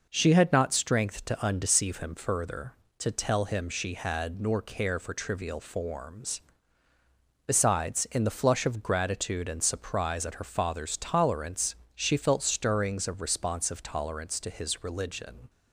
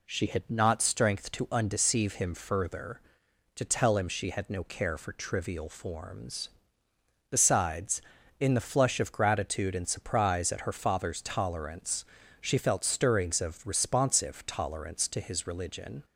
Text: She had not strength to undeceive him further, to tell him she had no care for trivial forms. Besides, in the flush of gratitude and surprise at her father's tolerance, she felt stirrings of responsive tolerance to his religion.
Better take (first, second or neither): second